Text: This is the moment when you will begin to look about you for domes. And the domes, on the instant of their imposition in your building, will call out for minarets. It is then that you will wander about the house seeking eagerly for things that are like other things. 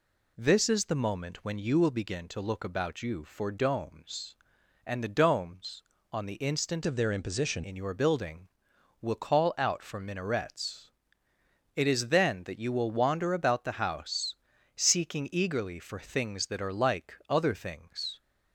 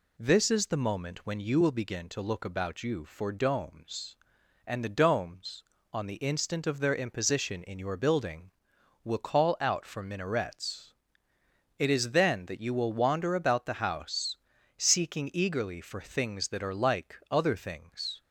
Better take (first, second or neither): second